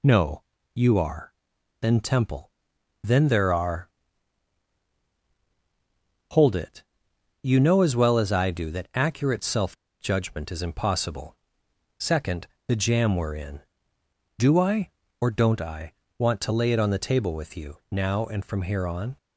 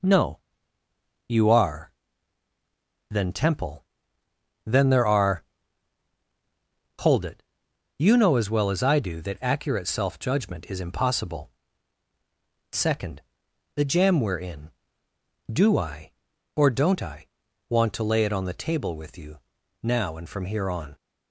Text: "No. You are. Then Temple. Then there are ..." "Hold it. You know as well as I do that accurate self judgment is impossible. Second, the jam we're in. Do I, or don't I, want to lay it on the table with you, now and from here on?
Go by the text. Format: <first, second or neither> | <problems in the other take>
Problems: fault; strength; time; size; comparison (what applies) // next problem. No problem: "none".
second | pauses between "self" and "judgment"; slight; at 9.7 s; 0.25 s long